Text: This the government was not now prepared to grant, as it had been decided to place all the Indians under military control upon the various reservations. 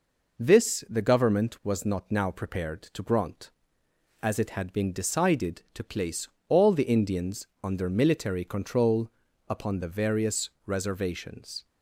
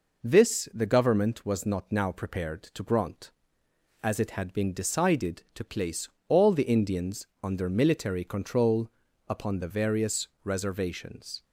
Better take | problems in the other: neither | pauses between "place" and "all"; slight; the same in both // pauses between "Indians" and "under"; slight; the same in both // pauses between "control" and "upon"; the same in both // pauses between "various" and "reservations"; slight; the same in both

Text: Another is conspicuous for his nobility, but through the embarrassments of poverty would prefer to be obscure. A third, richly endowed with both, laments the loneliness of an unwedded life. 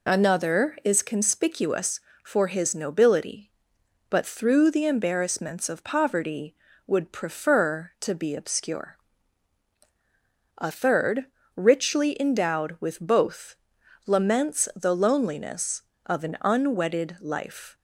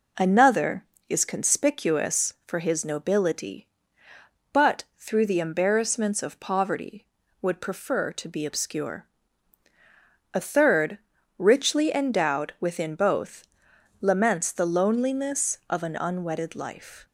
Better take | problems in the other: first | says "within" for "with"; at 12.5 s

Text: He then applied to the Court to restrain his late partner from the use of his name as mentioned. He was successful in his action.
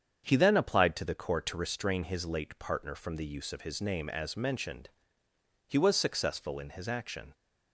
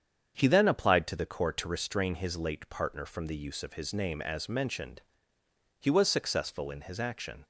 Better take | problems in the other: neither | starts louder than the rest; strong; the same in both

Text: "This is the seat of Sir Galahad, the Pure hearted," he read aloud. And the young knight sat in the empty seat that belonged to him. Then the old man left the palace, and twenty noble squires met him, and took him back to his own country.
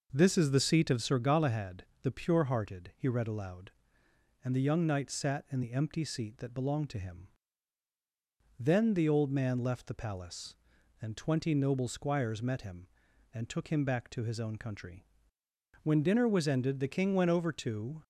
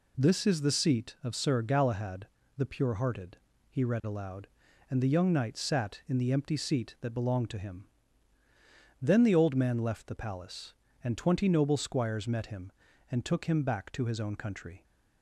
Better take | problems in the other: second | goes on to say "When dinner was ended the King went over to"; strong; from 15.8 s on; 2.1 s long

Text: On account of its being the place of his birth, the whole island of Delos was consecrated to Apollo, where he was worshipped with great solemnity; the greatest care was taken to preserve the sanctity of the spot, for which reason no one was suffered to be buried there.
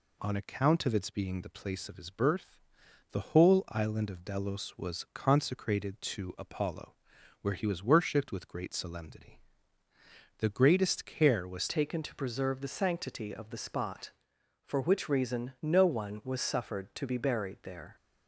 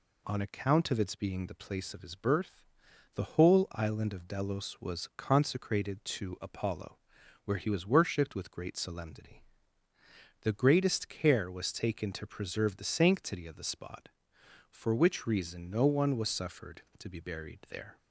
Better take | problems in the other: second | changes voice at "taken"; from 11.6 s on; 6.3 s long

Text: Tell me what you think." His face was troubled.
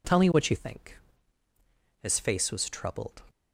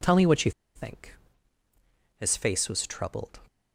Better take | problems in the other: first | pauses between "you" and "think"; slight; at 0.5 s; 0.25 s long

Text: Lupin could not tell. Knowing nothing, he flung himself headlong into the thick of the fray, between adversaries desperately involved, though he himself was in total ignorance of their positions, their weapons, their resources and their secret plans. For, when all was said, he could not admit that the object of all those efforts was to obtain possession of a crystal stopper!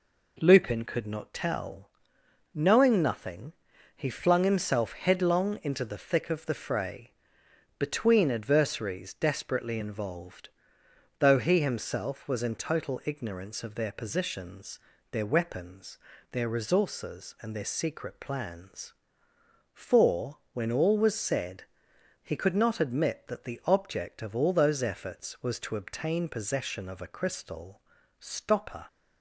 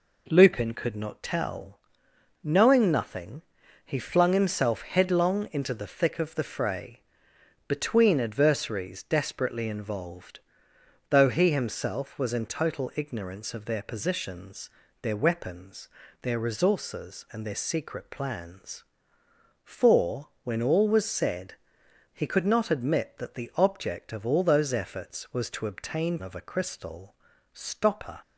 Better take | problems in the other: first | skips "possession"; at 26.2 s // pauses between "crystal" and "stopper"; at 27.1 s; 0.40 s long; also in the first

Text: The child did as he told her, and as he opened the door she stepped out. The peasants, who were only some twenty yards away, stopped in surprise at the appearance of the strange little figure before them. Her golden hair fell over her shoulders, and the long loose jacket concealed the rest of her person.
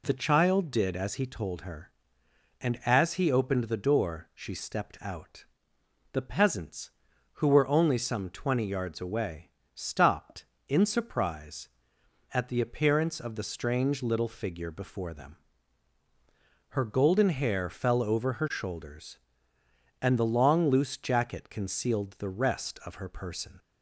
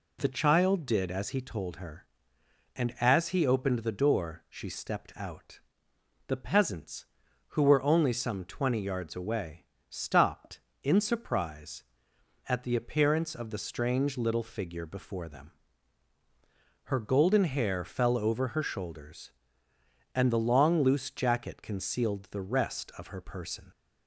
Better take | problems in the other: neither | none

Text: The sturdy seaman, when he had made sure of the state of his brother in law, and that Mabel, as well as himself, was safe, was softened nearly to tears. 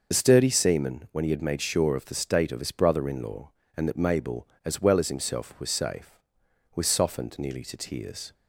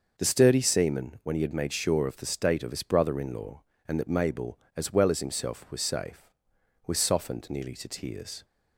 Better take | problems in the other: second | loses the start of "The"; at 0.1 s; 35 ms

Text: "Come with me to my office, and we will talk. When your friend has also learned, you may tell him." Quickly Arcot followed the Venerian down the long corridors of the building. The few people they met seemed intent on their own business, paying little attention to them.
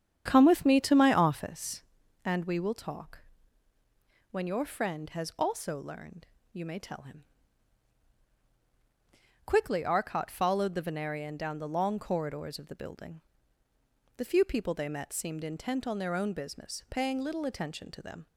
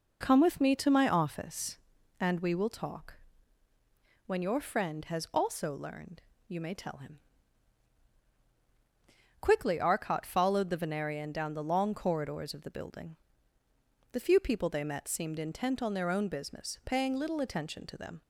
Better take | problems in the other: second | starts louder than the rest; strong; until 1.6 s; 8.5 dB

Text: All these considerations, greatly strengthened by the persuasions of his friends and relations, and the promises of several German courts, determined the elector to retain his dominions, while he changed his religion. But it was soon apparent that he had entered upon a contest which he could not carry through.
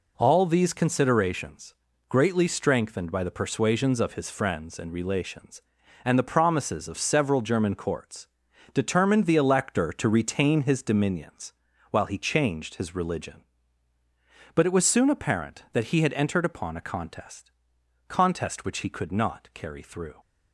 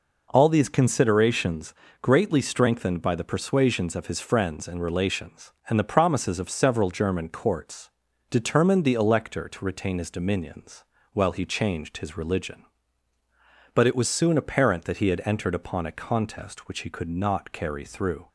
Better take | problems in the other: second | says "contest" twice; at 18.0 s

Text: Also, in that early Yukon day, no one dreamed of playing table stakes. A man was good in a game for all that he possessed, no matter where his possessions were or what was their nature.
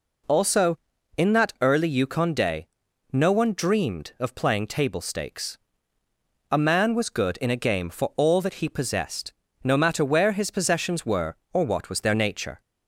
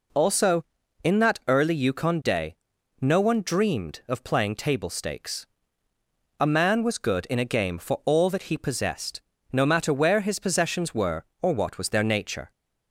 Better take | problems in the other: neither | none

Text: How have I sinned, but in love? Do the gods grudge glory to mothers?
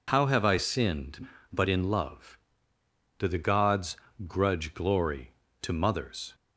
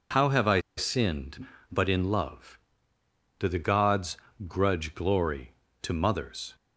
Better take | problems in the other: first | pauses between "I" and "sinned"; slight; at 0.5 s; 0.17 s long // pauses between "gods" and "grudge"; slight; at 4.1 s; 0.28 s long; slight in the first

